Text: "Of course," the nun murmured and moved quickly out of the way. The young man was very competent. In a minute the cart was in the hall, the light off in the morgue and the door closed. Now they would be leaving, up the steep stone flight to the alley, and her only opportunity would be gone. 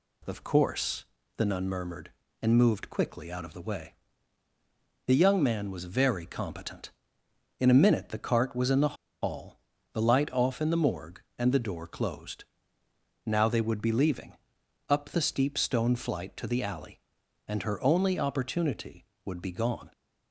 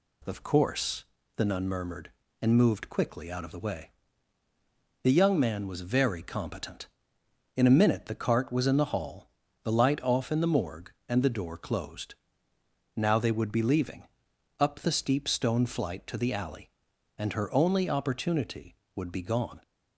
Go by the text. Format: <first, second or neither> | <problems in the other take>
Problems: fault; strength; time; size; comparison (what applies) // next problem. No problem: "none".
second | pauses between "the" and "hall"; slight; at 8.9 s; 0.27 s long